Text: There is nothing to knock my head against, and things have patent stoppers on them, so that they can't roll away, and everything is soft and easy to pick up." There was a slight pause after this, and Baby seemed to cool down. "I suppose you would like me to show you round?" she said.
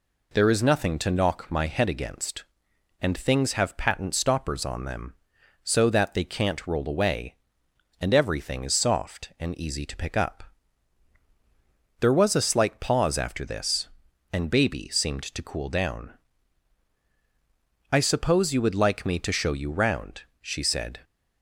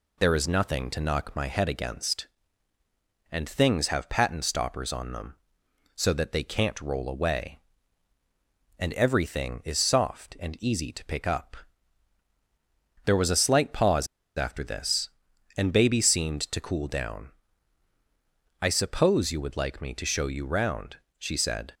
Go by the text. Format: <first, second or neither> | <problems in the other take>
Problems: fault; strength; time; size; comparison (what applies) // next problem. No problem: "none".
first | pauses between "pause" and "after"; slight; at 14.0 s; 0.30 s long